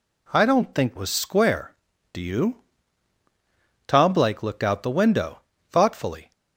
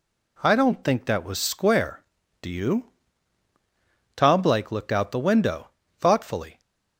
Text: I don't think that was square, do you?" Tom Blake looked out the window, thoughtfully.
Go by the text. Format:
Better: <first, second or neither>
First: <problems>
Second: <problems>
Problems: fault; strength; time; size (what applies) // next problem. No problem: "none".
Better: second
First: skips "that"; at 0.9 s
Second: none